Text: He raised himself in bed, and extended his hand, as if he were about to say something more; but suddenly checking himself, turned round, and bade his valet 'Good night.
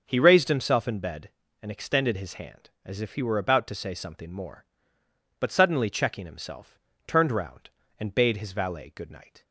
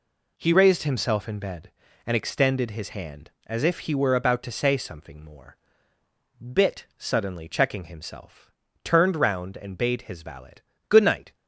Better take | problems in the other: first | says "bit" for "but"; at 6.4 s // pauses between "valet" and "Good"; slight; at 10.5 s; 0.36 s long

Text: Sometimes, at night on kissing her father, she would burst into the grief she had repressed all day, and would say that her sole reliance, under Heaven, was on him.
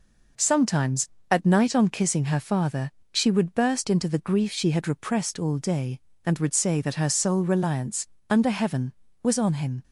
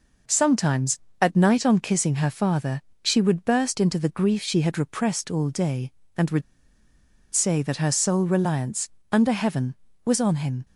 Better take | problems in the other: first | pauses between "would" and "say"; noticeable; at 6.4 s; 0.92 s long

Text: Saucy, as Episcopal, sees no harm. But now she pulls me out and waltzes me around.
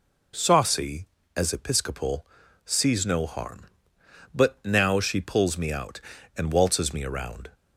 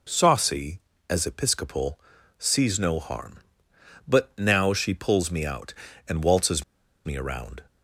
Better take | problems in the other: first | pauses between "waltzes" and "me"; at 6.6 s; 0.41 s long

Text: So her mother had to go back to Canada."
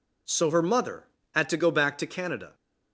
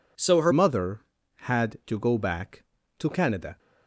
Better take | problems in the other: first | changes voice at "mother"; from 0.5 s on; 3.0 s long

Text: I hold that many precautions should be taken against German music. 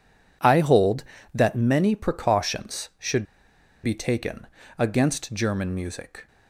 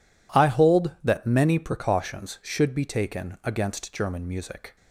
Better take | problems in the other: second | pauses between "should" and "be"; noticeable; at 3.2 s; 0.58 s long // pauses between "taken" and "against"; slight; at 4.4 s; 0.32 s long

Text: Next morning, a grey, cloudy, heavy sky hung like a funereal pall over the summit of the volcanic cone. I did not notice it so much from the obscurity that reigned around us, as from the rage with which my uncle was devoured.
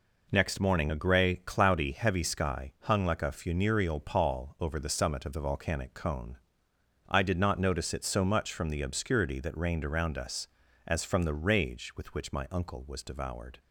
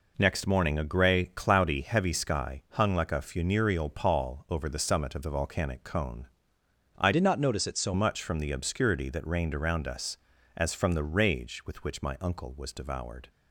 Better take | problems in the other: first | changes voice from "did" to "so"; from 7.1 to 7.9 s; 0.8 s long

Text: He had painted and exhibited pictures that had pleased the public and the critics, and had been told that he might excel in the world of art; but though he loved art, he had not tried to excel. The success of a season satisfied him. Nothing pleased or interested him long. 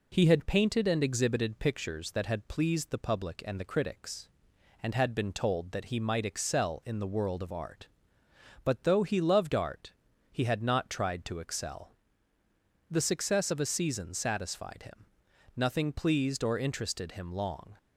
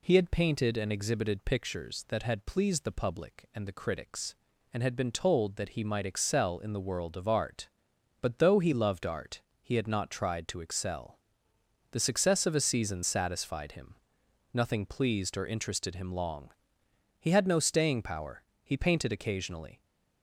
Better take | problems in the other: first | goes on to say "He had no staying power He painted occasionally"; strong; from 17.1 s on; 2.6 s long

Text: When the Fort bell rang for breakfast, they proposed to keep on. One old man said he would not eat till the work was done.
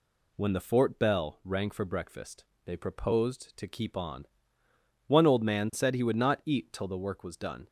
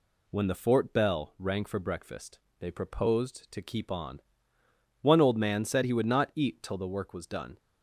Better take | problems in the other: neither | none

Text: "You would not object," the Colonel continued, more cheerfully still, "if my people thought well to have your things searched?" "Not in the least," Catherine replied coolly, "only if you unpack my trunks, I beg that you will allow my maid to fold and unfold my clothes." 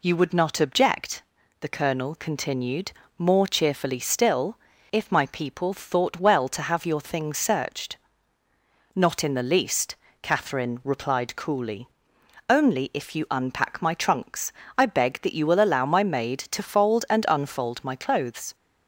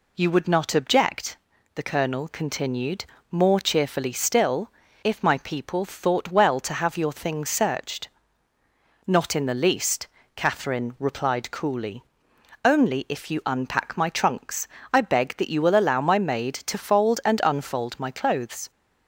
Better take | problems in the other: neither | none

